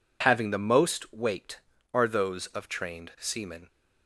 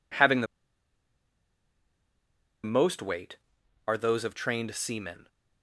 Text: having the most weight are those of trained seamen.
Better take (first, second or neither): first